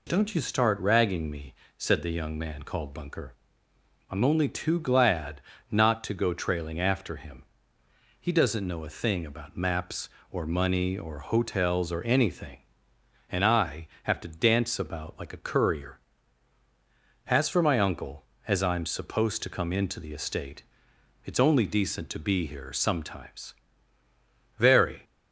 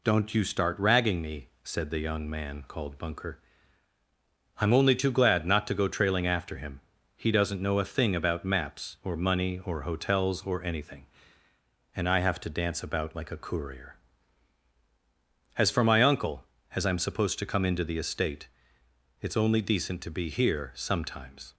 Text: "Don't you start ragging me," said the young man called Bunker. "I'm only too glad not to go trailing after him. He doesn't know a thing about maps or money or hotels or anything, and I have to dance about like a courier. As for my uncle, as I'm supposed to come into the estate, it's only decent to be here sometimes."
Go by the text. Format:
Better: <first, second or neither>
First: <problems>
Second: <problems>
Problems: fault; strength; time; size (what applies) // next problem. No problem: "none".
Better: second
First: pauses between "glad" and "not"; slight; at 5.4 s; 0.28 s long // goes on to say "Very"; slight; from 24.5 s on; 0.46 s long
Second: none